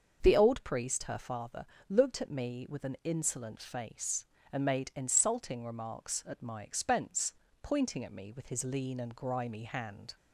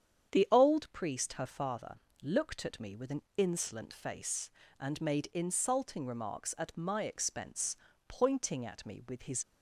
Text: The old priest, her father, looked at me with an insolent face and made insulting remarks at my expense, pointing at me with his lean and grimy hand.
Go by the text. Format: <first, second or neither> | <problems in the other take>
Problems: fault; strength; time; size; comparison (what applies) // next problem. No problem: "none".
first | starts louder than the rest; strong; until 1.3 s; 8 dB; also in the first // pauses between "an" and "insolent"; slight; at 3.2 s; 0.16 s long // stops before "lean and grimy hand"; at 9.4 s